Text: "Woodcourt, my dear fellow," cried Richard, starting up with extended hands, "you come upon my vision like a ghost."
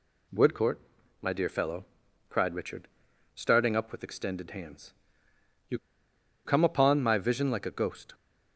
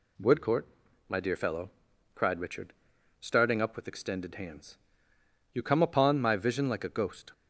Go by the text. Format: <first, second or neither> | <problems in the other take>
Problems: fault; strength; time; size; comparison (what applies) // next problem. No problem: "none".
second | pauses between "you" and "come"; noticeable; at 5.7 s; 0.67 s long